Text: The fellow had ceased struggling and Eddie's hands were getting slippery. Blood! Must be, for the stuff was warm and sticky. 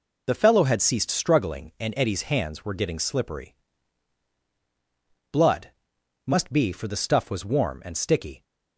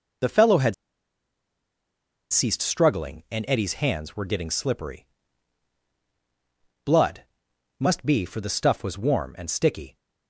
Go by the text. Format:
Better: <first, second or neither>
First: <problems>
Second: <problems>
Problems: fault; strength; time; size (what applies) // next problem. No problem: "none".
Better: first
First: none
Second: pauses between "had" and "ceased"; strong; at 0.7 s; 1.5 s long